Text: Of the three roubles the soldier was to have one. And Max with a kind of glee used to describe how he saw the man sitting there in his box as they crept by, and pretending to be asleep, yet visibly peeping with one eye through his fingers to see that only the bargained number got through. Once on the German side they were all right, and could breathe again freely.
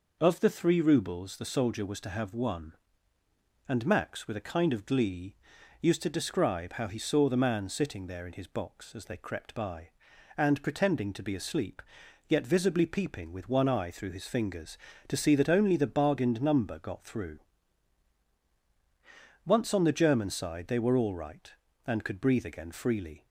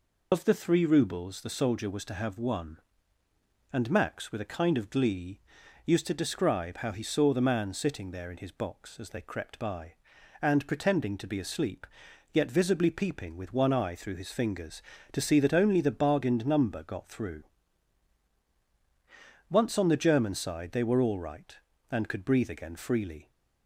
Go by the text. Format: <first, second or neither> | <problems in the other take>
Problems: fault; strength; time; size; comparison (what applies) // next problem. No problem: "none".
first | loses the start of "Of"; at 0.3 s; 75 ms // pauses between "glee" and "used"; noticeable; at 5.3 s; 0.48 s long; noticeable in the first